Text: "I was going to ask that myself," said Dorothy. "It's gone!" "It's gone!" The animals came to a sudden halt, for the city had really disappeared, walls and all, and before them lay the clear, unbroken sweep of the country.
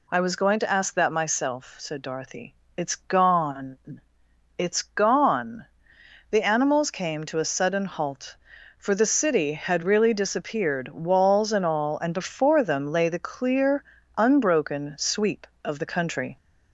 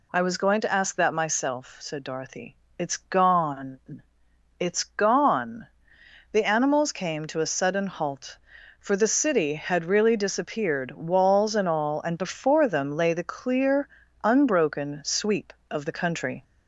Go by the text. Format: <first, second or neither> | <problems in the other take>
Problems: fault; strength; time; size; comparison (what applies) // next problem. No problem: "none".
neither | none